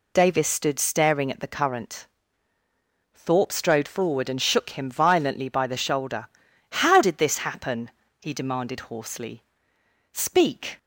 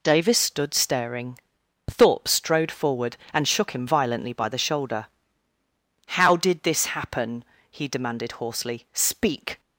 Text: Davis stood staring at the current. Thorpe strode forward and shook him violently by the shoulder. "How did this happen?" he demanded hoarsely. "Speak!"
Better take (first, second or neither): first